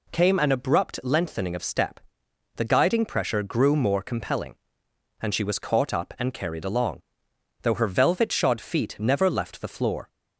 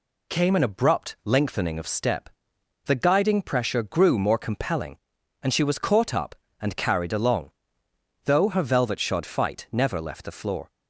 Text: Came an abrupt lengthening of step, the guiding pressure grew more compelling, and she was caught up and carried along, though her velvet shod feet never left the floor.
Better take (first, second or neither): first